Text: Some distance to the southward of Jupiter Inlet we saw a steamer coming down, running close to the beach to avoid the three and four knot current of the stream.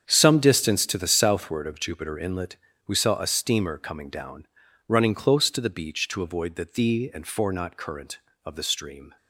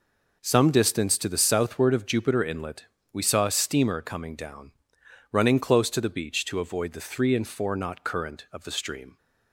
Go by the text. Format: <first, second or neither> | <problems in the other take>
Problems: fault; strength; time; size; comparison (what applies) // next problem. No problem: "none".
second | starts louder than the rest; strong; until 1.0 s; 8 dB // pauses between "Inlet" and "we"; slight; at 2.5 s; 0.32 s long; slight in the second // says "thee" for "three"; at 6.6 s